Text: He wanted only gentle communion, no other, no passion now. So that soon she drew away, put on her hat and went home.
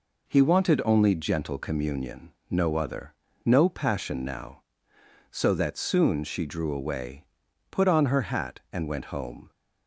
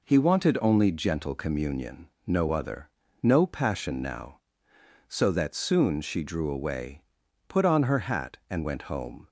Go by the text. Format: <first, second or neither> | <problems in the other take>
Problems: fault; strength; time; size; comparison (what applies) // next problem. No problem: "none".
neither | none